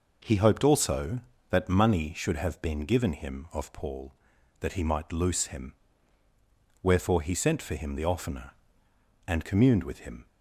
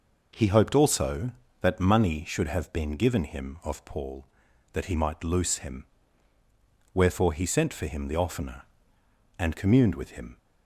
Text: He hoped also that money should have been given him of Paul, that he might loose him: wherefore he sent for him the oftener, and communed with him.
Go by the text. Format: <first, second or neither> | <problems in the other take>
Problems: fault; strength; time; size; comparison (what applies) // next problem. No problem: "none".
neither | none